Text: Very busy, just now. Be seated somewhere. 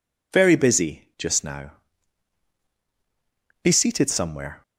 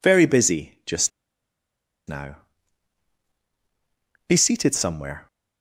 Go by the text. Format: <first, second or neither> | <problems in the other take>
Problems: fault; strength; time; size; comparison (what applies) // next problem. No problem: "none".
first | pauses between "just" and "now"; noticeable; at 1.0 s; 0.97 s long